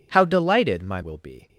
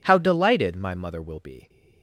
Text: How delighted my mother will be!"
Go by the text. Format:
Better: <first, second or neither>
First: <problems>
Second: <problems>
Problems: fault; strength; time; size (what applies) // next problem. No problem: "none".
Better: second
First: skips "mother"; at 1.0 s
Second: none